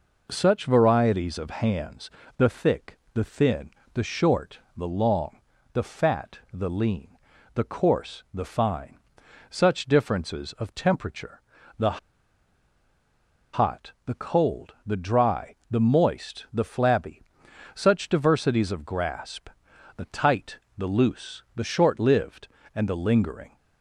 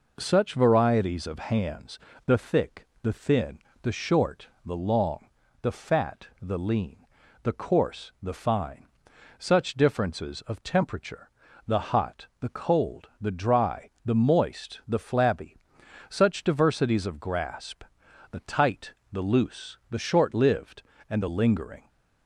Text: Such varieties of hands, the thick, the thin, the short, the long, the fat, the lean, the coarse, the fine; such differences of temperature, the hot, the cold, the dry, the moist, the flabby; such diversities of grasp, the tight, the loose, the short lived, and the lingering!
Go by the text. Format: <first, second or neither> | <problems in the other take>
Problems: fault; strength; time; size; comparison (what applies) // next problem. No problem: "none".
second | pauses between "the" and "hot"; strong; at 11.9 s; 1.5 s long